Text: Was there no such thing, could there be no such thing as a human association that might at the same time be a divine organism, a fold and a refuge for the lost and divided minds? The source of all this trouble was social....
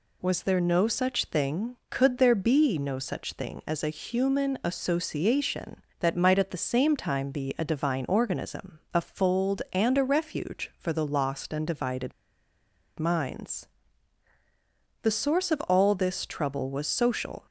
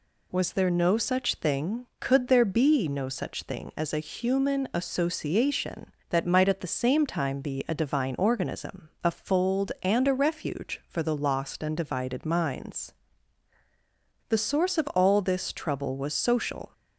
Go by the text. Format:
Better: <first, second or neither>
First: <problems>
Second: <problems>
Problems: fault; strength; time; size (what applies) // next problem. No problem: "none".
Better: second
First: pauses between "divided" and "minds"; noticeable; at 12.1 s; 0.87 s long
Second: none